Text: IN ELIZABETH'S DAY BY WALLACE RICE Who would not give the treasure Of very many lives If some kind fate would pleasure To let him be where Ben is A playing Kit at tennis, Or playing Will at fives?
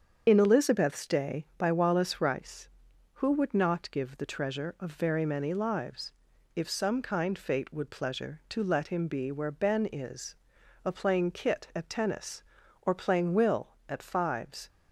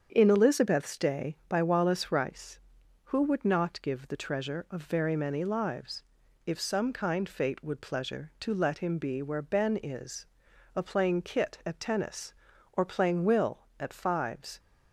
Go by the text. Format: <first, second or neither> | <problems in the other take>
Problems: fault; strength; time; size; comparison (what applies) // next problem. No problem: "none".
second | loses the start of "IN"; at 0.2 s; 70 ms // starts louder than the rest; strong; until 1.2 s; 7.5 dB; strong in the second // pauses between "lives" and "If"; at 6.1 s; 0.42 s long; also in the second // pauses between "is" and "A"; noticeable; at 10.3 s; 0.50 s long; noticeable in the second